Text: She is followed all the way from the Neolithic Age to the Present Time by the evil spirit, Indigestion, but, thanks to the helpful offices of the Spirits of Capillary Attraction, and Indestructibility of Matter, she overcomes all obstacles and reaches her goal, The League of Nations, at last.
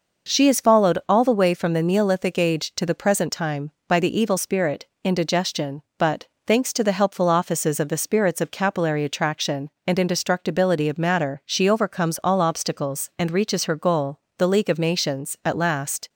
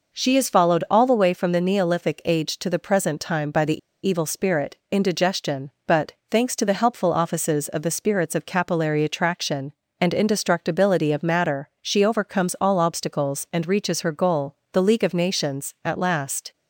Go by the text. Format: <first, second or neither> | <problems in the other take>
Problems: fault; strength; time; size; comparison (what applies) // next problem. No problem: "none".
first | pauses between "the" and "evil"; slight; at 3.7 s; 0.26 s long